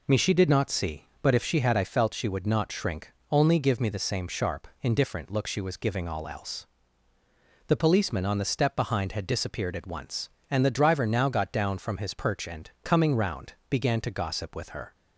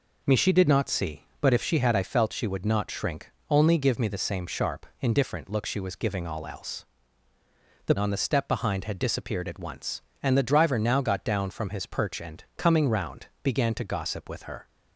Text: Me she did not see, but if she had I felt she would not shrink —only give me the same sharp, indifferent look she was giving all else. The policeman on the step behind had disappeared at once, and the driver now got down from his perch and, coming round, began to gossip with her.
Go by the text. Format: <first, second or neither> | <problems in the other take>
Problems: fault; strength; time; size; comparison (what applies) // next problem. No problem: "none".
first | skips "policeman"; at 7.9 s